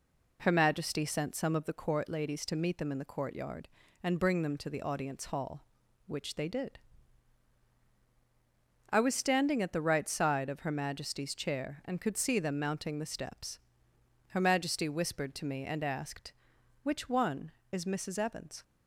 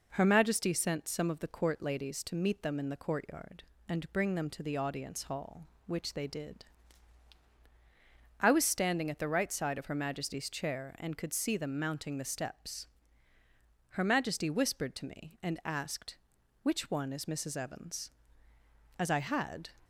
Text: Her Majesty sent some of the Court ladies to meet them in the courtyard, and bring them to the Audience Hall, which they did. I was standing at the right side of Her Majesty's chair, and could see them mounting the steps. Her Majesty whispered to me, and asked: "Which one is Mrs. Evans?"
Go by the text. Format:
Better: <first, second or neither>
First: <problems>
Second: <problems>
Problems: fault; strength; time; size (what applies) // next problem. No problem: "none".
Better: first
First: none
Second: goes on to say "As I had"; noticeable; from 18.9 s on; 0.70 s long